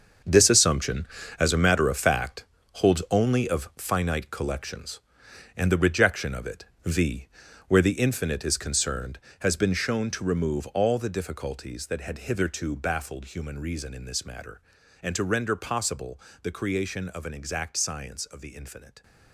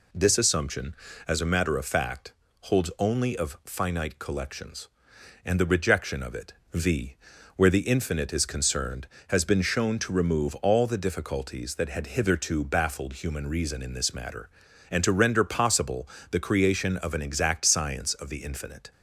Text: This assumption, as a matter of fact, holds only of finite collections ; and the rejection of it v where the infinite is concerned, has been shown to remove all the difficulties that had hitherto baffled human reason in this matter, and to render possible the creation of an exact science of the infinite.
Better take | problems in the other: second | gets quieter; strong; throughout; 12 dB // pauses between "it" and "v"; slight; at 6.6 s; 0.20 s long; slight in the second // pauses between "v" and "where"; at 7.2 s; 0.40 s long; also in the second // pauses between "possible" and "the"; slight; at 16.2 s; 0.22 s long; slight in the second

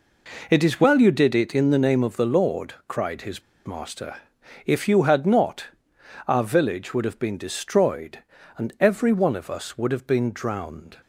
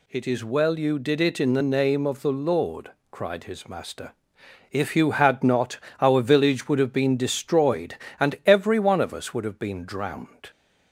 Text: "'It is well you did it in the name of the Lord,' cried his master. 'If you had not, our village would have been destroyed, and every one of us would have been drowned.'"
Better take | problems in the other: second | pauses between "his" and "master"; slight; at 3.4 s; 0.26 s long

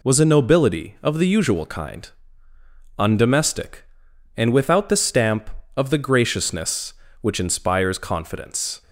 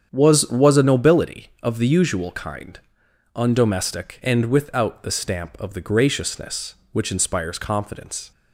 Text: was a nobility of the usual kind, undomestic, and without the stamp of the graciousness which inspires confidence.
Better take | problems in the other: first | starts louder than the rest; strong; until 1.1 s; 8 dB // says "was" twice; at 0.5 s

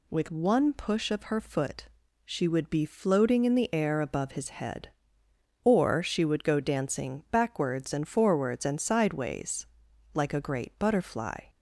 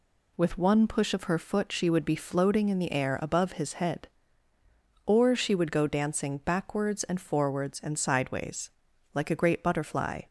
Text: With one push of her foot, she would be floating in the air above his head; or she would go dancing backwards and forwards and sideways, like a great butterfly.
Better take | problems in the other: neither | none

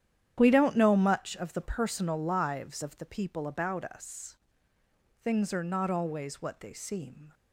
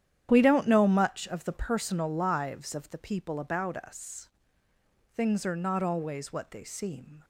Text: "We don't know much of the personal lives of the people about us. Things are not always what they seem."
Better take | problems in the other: neither | starts louder than the rest; strong; the same in both

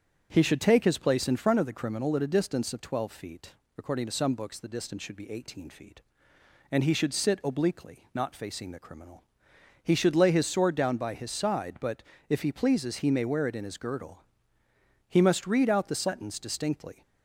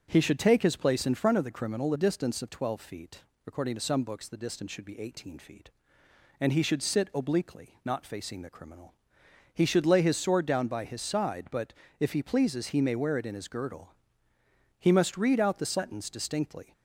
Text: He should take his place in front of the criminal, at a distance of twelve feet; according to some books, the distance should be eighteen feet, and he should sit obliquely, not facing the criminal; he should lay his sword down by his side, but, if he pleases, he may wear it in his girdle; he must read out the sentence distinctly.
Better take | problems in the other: first | starts louder than the rest; until 1.1 s; 7 dB; strong in the first // skips "at"; at 1.9 s

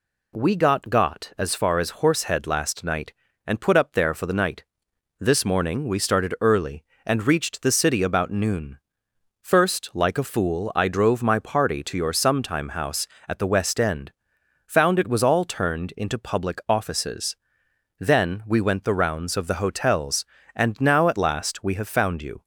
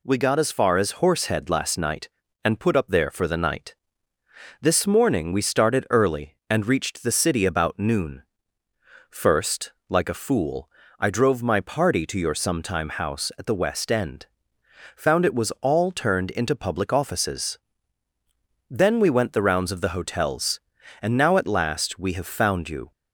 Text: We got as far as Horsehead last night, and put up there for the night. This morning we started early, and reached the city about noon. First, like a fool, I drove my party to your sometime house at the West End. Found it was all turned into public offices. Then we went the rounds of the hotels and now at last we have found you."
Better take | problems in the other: second | says "got" twice; at 0.9 s

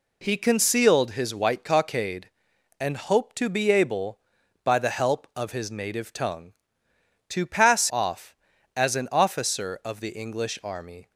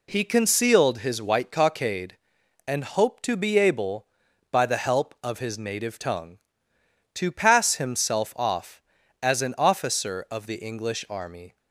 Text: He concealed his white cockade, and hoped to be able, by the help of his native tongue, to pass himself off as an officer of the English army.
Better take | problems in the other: second | skips "himself"; at 7.8 s

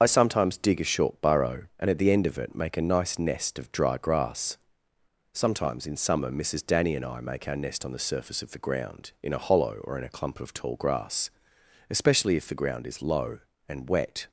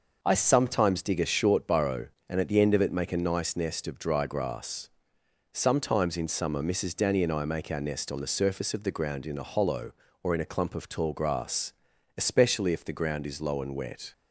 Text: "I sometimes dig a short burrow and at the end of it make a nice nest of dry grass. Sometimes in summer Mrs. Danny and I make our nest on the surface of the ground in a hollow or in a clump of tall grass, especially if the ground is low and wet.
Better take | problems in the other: second | loses the start of "I"; at 0.0 s; 35 ms // starts louder than the rest; until 1.0 s; 6.5 dB

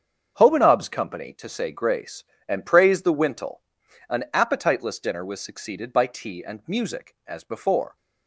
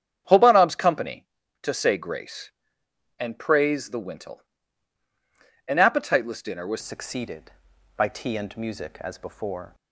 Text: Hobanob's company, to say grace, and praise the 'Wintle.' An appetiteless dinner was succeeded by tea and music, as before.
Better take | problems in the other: first | starts louder than the rest; strong; until 1.6 s; 8.5 dB; strong in the first // changes voice at "succeeded"; from 6.8 s on; 2.9 s long

